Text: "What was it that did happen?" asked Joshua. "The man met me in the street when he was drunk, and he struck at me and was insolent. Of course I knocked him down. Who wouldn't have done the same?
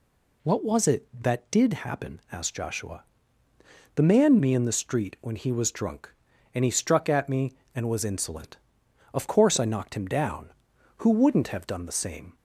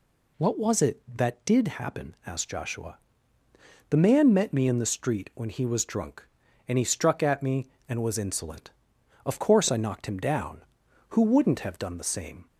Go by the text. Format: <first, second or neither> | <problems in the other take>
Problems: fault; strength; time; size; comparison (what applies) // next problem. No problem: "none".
second | skips "met"; at 4.3 s